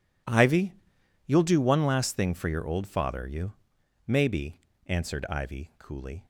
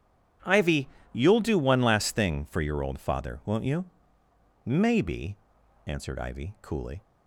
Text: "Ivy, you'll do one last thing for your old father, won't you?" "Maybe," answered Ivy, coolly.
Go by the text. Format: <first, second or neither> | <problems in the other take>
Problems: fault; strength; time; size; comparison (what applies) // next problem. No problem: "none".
second | skips "won't"; at 3.2 s